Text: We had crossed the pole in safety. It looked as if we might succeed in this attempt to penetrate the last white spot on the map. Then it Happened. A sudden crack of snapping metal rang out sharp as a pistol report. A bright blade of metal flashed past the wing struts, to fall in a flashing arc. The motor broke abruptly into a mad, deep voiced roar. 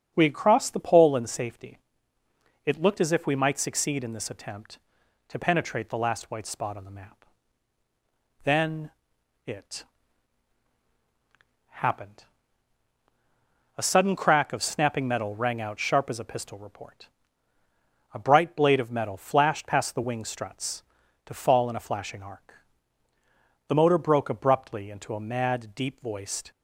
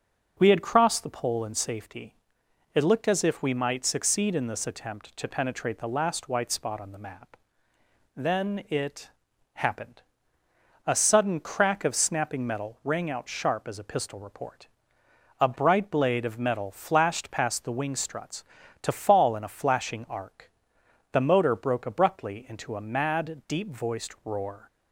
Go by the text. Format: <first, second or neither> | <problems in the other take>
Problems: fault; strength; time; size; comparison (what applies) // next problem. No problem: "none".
second | starts louder than the rest; until 1.1 s; 7 dB; also in the second // pauses between "Then" and "it"; noticeable; at 8.9 s; 0.54 s long // pauses between "it" and "Happened"; strong; at 9.8 s; 1.8 s long; also in the second // stops before "roar"; at 26.5 s